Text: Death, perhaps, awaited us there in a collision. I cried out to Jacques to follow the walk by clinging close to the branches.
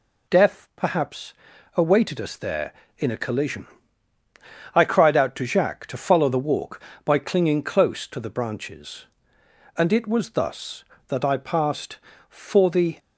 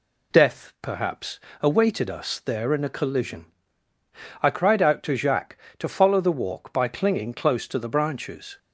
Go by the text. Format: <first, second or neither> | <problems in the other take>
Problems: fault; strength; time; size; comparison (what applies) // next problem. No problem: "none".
second | goes on to say "And it was thus that I passed for the"; strong; from 9.7 s on; 3.2 s long